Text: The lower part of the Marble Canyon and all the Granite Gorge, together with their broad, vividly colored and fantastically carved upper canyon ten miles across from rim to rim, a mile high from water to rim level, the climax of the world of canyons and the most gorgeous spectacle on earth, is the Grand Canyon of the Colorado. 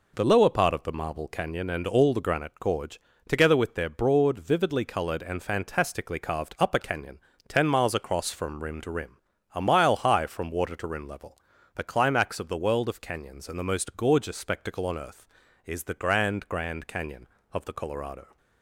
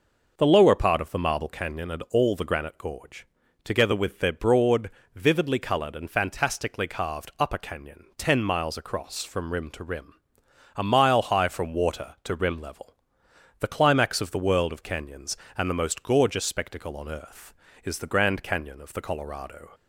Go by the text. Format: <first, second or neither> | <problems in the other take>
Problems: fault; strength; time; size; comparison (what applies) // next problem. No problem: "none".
second | pauses between "canyon" and "ten"; slight; at 7.1 s; 0.30 s long // says "Grand" twice; at 16.4 s